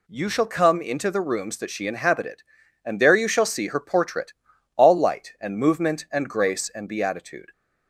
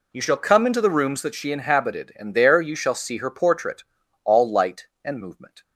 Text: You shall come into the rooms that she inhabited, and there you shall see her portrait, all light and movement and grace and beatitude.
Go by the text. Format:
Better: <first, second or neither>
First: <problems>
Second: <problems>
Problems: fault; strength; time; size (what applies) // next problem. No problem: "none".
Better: first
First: none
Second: stops before "and grace and beatitude"; at 5.6 s